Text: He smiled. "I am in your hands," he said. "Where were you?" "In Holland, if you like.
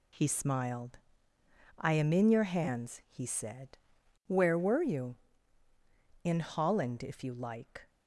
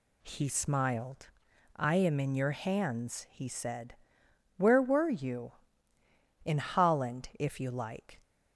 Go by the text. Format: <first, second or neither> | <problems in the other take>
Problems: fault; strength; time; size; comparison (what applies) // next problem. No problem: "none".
neither | none